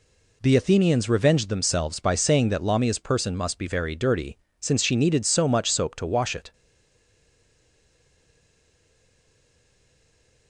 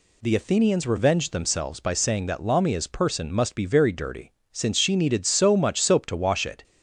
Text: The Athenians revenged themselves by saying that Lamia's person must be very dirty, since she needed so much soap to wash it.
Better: second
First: stays silent after the last word; strong; from 6.5 s on; 3.9 s long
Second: none

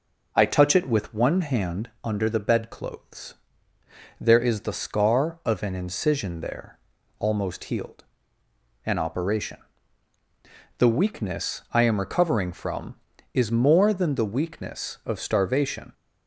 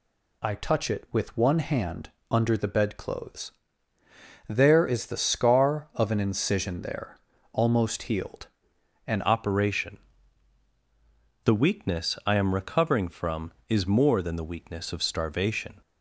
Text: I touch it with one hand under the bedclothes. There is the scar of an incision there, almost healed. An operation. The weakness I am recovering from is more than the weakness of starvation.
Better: first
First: none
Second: pauses between "hand" and "under"; slight; at 2.1 s; 0.20 s long // changes voice at "operation"; from 9.2 s on; 6.6 s long

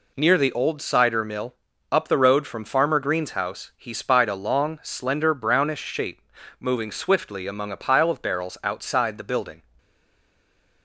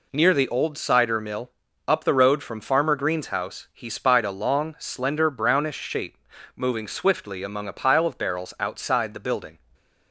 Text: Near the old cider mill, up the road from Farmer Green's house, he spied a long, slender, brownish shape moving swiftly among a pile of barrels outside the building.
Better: second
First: pauses between "shape" and "moving"; at 6.1 s; 0.40 s long // stays silent after the last word; from 9.7 s on; 1.1 s long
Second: pauses between "shape" and "moving"; at 6.1 s; 0.40 s long

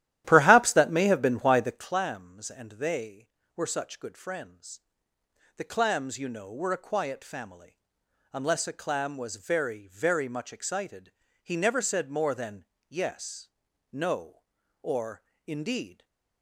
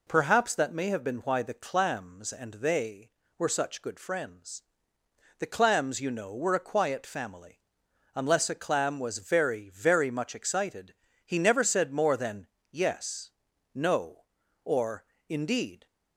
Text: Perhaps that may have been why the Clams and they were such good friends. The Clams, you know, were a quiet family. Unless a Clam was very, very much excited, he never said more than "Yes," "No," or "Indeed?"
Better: second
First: starts louder than the rest; strong; until 2.0 s; 13 dB // pauses between "than" and "Yes"; slight; at 12.6 s; 0.26 s long // pauses between "or" and "Indeed"; slight; at 15.2 s; 0.24 s long // stays silent after the last word; slight; from 15.9 s on; 0.5 s long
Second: pauses between "than" and "Yes"; slight; at 12.4 s; 0.26 s long // pauses between "or" and "Indeed"; slight; at 15.0 s; 0.24 s long

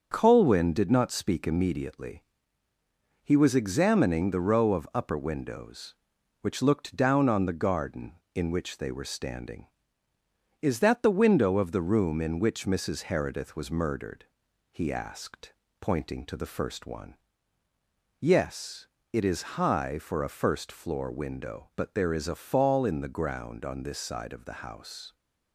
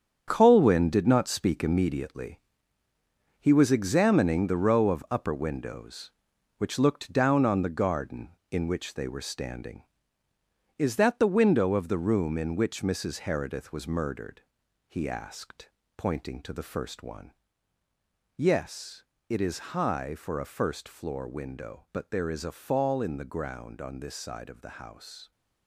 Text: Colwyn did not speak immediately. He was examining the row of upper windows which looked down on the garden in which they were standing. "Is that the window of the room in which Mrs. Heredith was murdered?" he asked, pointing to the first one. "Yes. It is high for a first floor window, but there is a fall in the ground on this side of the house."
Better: first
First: starts louder than the rest; until 1.1 s; 7 dB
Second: gets quieter; strong; throughout; 10.5 dB // starts louder than the rest; strong; until 1.2 s; 8 dB

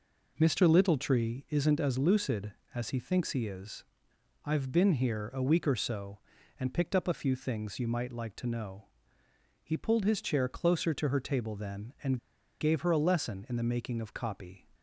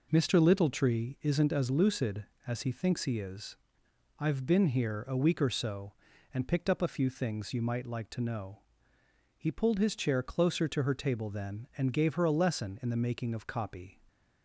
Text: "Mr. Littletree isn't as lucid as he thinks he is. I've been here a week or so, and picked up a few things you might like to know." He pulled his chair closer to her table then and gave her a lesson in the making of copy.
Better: second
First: pauses between "and" and "gave"; at 12.1 s; 0.42 s long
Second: none

